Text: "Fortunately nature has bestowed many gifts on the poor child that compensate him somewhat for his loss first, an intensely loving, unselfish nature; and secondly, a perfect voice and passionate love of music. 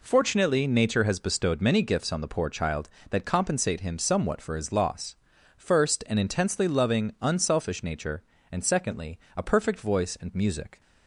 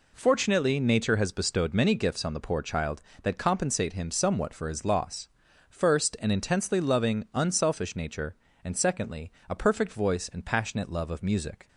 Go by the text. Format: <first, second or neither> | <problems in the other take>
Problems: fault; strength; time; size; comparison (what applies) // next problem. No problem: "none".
second | pauses between "loss" and "first"; at 5.1 s; 0.42 s long; also in the second // skips "passionate love of"; at 10.3 s